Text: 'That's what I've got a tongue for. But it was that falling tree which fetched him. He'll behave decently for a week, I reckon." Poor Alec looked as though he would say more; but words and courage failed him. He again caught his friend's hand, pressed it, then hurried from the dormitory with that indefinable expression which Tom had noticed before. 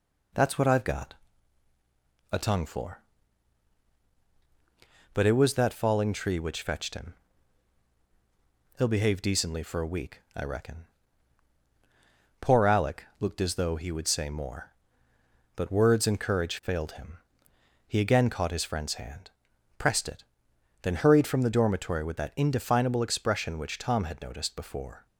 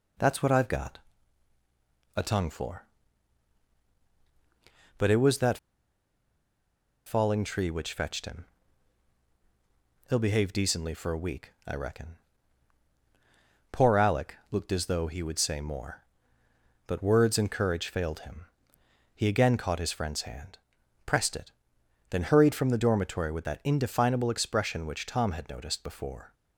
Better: first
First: pauses between "got" and "a"; at 1.1 s; 1.1 s long // pauses between "Alec" and "looked"; slight; at 13.0 s; 0.16 s long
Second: pauses between "got" and "a"; at 0.9 s; 1.1 s long // pauses between "that" and "falling"; strong; at 5.5 s; 1.4 s long // pauses between "Alec" and "looked"; slight; at 14.3 s; 0.16 s long

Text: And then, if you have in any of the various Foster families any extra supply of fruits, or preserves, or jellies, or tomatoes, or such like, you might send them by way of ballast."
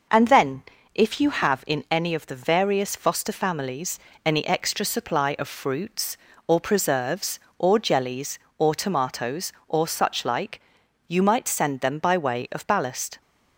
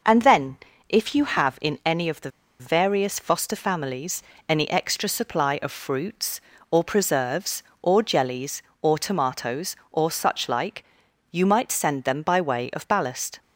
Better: first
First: pauses between "families" and "any"; slight; at 3.9 s; 0.26 s long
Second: pauses between "the" and "various"; slight; at 2.3 s; 0.29 s long // pauses between "families" and "any"; slight; at 4.2 s; 0.26 s long

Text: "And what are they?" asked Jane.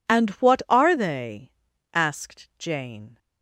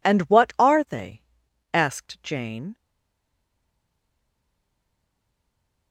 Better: first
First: none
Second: stays silent after the last word; strong; from 2.7 s on; 3.2 s long

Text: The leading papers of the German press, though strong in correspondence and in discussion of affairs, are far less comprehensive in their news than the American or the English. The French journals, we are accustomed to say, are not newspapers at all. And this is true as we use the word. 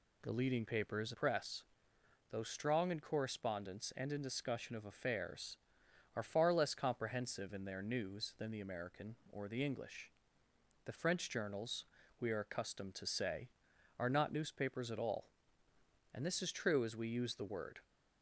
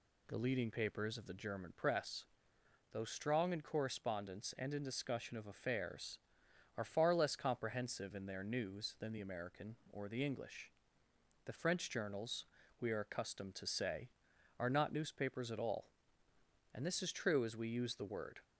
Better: second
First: skips "of the German"; at 1.1 s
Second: none

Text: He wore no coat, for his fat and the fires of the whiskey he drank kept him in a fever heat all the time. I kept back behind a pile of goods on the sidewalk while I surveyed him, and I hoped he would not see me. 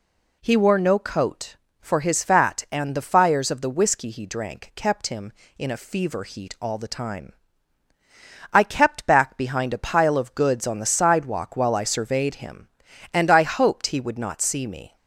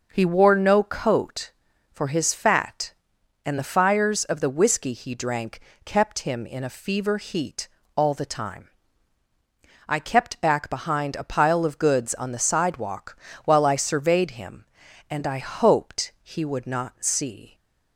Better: first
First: none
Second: pauses between "drank" and "kept"; slight; at 5.5 s; 0.26 s long // pauses between "heat" and "all"; slight; at 7.6 s; 0.28 s long // pauses between "sidewalk" and "while"; slight; at 13.1 s; 0.28 s long // stops before "me"; at 17.5 s

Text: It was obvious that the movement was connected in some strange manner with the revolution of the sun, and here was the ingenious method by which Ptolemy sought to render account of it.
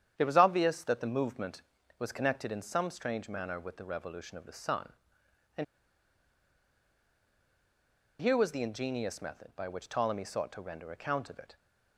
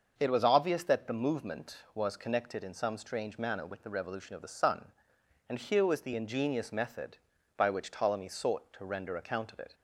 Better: second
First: starts louder than the rest; strong; until 1.2 s; 9.5 dB // pauses between "and" and "here"; strong; at 5.6 s; 2.5 s long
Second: starts louder than the rest; noticeable; until 1.2 s; 6 dB

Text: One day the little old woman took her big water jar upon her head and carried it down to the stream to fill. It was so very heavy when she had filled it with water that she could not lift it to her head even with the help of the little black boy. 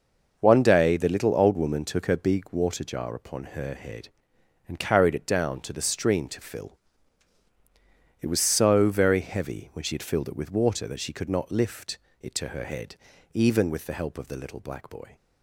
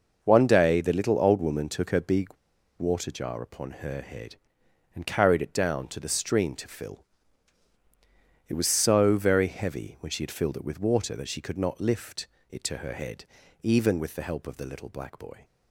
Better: first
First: pauses between "lift" and "it"; slight; at 11.9 s; 0.22 s long // pauses between "head" and "even"; slight; at 12.9 s; 0.36 s long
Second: pauses between "big" and "water"; noticeable; at 2.2 s; 0.51 s long // pauses between "lift" and "it"; slight; at 12.2 s; 0.22 s long // pauses between "head" and "even"; slight; at 13.2 s; 0.36 s long

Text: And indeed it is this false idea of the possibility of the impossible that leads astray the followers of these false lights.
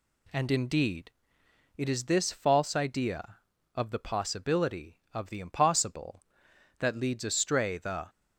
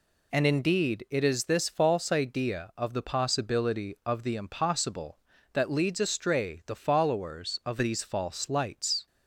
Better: second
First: pauses between "indeed" and "it"; noticeable; at 1.1 s; 0.66 s long // stops before "followers of these false lights"; at 8.0 s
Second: none

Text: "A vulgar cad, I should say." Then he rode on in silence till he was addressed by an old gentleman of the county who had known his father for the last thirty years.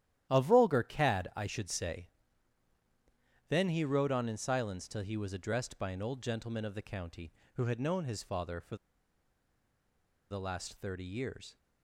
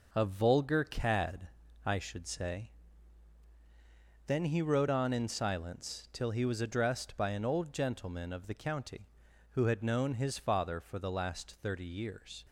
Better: second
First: starts louder than the rest; strong; until 1.3 s; 12 dB // pauses between "for" and "the"; strong; at 8.7 s; 1.5 s long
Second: none

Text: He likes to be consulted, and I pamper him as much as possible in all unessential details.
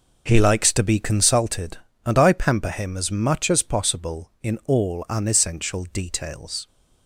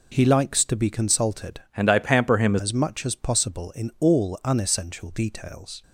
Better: first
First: none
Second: changes voice from "and" to "him"; from 1.7 to 2.5 s; 0.8 s long

